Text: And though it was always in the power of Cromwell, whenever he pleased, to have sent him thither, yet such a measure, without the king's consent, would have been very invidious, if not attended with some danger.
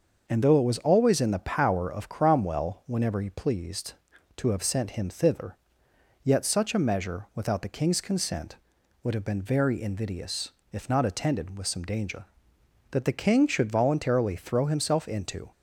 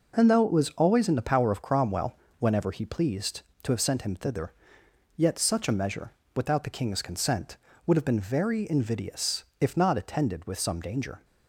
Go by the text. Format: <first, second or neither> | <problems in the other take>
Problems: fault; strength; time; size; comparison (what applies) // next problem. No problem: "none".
second | starts louder than the rest; until 1.2 s; 6 dB // goes on to say "That the king should voluntarily throw himself into"; strong; from 12.9 s on; 2.5 s long